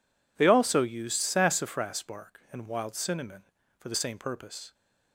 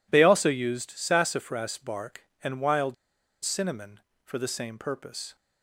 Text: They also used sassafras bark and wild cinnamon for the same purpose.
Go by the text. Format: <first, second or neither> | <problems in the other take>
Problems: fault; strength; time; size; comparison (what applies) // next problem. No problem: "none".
first | pauses between "wild" and "cinnamon"; noticeable; at 2.9 s; 0.48 s long